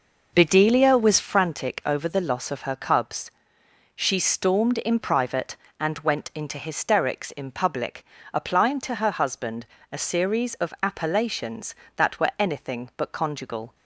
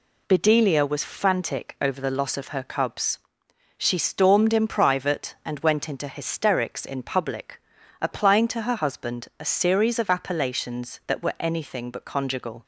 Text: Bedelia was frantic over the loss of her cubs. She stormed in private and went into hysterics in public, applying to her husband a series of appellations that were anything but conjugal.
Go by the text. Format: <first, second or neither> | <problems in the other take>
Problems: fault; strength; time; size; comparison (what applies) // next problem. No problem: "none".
second | starts louder than the rest; noticeable; until 1.3 s; 5 dB // pauses between "husband" and "a"; slight; at 9.6 s; 0.24 s long